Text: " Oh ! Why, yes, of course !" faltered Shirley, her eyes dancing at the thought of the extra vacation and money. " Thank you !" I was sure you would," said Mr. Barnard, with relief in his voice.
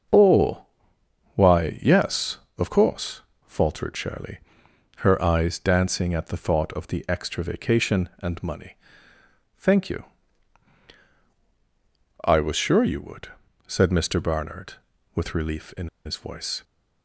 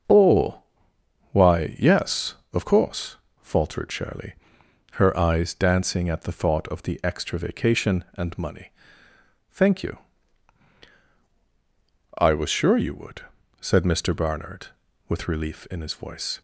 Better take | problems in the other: second | starts louder than the rest; strong; until 1.7 s; 7.5 dB; strong in the second // pauses between "in" and "his"; slight; at 15.8 s; 0.18 s long

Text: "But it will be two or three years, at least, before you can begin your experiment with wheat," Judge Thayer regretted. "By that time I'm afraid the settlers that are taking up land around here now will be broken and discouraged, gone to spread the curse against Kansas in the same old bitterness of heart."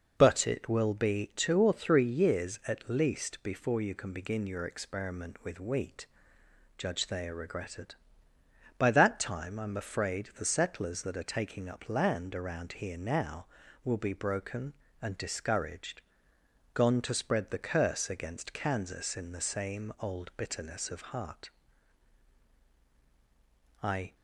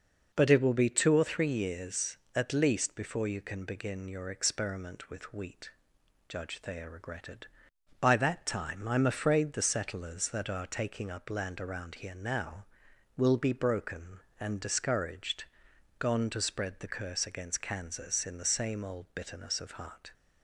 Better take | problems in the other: second | goes on to say "I"; slight; from 23.8 s on; 0.32 s long

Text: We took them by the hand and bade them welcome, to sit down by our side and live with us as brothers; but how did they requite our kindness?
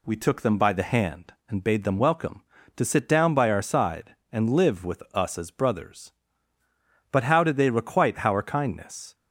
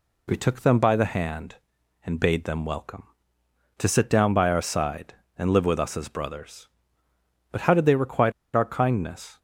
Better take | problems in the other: first | pauses between "requite" and "our"; slight; at 8.3 s; 0.23 s long

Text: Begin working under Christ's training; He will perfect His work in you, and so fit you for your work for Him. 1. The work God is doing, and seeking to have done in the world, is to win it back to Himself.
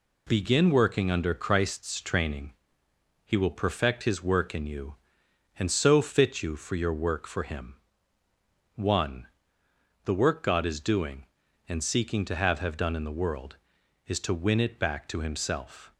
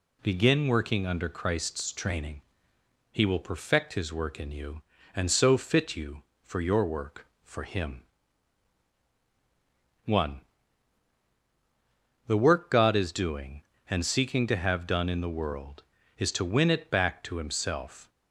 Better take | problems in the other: second | says "have" twice; at 12.5 s

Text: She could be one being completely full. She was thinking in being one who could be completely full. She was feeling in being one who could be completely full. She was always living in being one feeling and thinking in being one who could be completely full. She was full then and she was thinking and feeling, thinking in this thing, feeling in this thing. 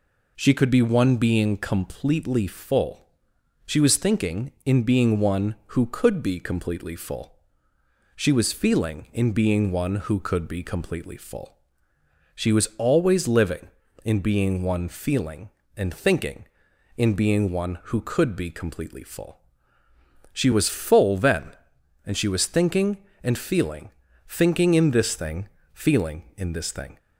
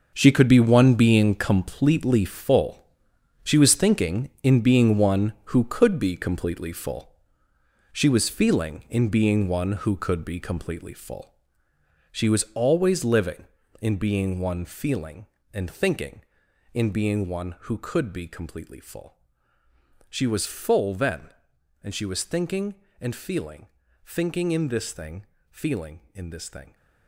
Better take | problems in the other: first | gets quieter; strong; throughout; 12 dB

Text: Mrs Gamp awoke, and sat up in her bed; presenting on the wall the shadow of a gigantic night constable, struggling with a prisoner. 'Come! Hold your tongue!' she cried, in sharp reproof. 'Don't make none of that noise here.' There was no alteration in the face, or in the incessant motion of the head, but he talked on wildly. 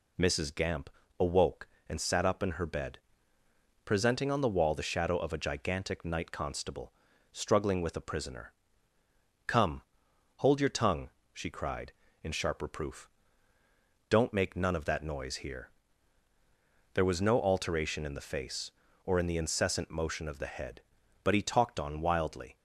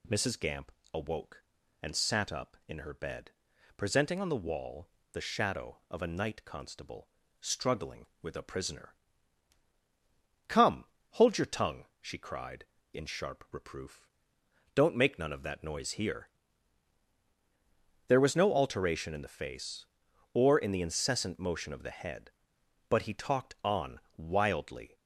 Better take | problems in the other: first | pauses between "Gamp" and "awoke"; slight; at 0.7 s; 0.22 s long; slight in the first // pauses between "wall" and "the"; slight; at 4.8 s; 0.26 s long // skips "gigantic"; at 6.0 s // pauses between "on" and "wildly"; slight; at 23.9 s; 0.16 s long

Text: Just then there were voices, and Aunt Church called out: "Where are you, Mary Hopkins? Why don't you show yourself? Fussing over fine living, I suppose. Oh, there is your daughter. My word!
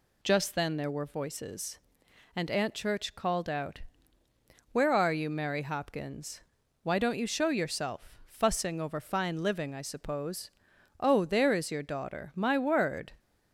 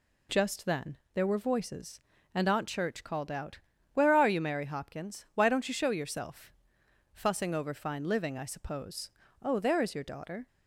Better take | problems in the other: first | pauses between "then" and "there"; slight; at 0.9 s; 0.18 s long // stops before "My word"; at 10.4 s

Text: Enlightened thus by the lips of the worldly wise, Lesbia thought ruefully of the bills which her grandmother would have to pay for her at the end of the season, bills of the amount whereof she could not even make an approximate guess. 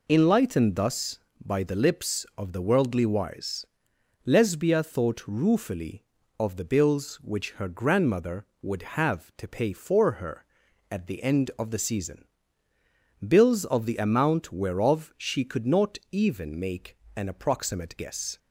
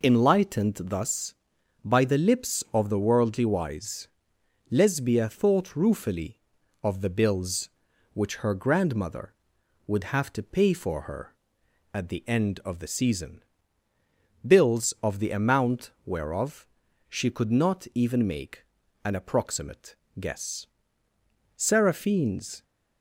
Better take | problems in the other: first | pauses between "amount" and "whereof"; slight; at 15.9 s; 0.16 s long // pauses between "whereof" and "she"; at 16.6 s; 0.42 s long // pauses between "make" and "an"; at 18.6 s; 0.38 s long; slight in the first // pauses between "approximate" and "guess"; slight; at 19.9 s; 0.22 s long // goes on to say "Seraphine's"; noticeable; from 21.5 s on; 1.0 s long

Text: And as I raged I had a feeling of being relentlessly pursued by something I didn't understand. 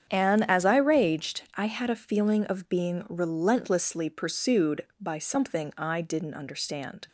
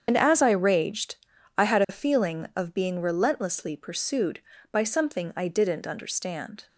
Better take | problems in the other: first | loses the start of "And"; at 0.0 s; 65 ms // starts louder than the rest; strong; until 1.0 s; 7.5 dB; strong in the first // pauses between "raged" and "I"; at 1.1 s; 0.40 s long; slight in the first

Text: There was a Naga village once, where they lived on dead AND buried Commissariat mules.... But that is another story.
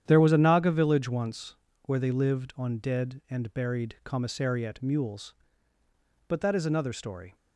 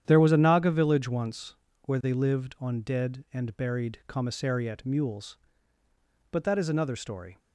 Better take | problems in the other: neither | starts louder than the rest; strong; the same in both

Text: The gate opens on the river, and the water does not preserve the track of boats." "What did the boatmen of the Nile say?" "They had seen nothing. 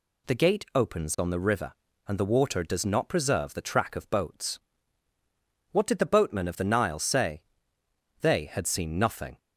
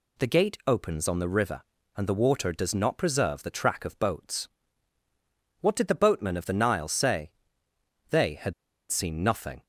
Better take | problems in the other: first | pauses between "had" and "seen"; at 8.5 s; 0.38 s long

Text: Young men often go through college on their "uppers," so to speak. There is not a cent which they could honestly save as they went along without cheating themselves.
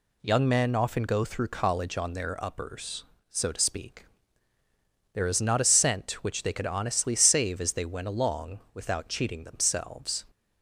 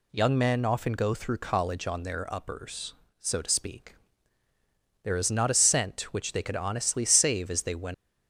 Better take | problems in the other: first | stops before "along without cheating themselves"; at 7.9 s

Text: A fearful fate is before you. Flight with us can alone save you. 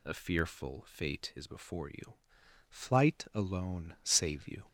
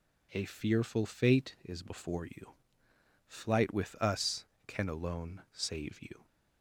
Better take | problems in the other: second | skips "with us can"; at 3.2 s

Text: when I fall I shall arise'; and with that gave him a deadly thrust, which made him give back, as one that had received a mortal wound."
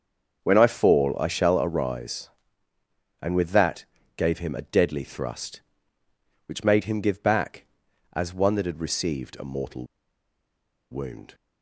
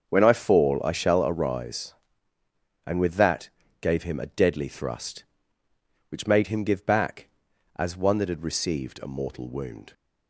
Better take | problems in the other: second | starts louder than the rest; until 1.4 s; 6.5 dB; also in the second // pauses between "that" and "gave"; slight; at 3.8 s; 0.32 s long; slight in the second // pauses between "mortal" and "wound"; at 9.8 s; 1.0 s long

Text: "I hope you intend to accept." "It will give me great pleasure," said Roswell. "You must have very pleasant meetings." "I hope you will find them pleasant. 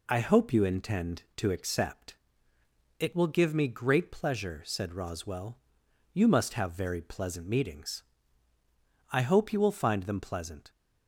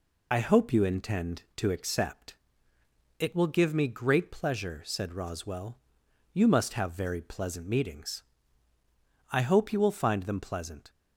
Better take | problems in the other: first | loses the start of "I"; at 0.3 s; 30 ms

